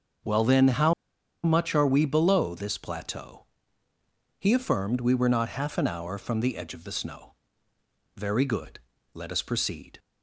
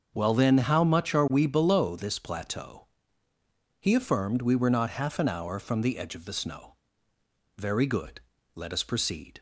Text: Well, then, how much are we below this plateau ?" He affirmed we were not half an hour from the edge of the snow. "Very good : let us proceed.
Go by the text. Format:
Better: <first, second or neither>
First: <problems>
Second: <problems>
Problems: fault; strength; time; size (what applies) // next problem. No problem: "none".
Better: second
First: starts louder than the rest; until 1.7 s; 6.5 dB // pauses between "how" and "much"; noticeable; at 0.9 s; 0.51 s long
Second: starts louder than the rest; until 1.1 s; 6 dB